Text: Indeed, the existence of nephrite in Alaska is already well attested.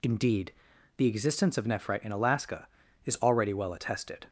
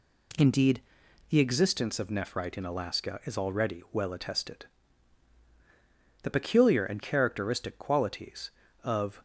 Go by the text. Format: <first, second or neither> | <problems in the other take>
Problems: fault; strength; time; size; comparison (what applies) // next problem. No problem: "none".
first | goes on to say "The peculiar and characteristic qualities of"; strong; from 6.2 s on; 3.0 s long